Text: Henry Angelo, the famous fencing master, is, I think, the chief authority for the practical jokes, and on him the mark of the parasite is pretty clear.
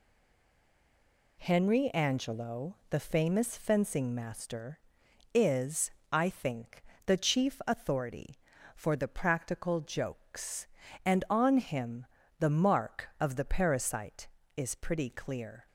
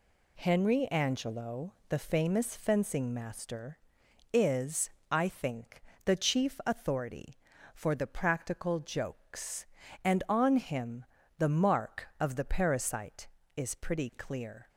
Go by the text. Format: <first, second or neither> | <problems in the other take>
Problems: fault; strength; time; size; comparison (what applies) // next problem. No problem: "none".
second | stays silent before the first word; noticeable; until 1.3 s; 1.3 s long // pauses between "him" and "the"; slight; at 12.0 s; 0.34 s long; slight in the second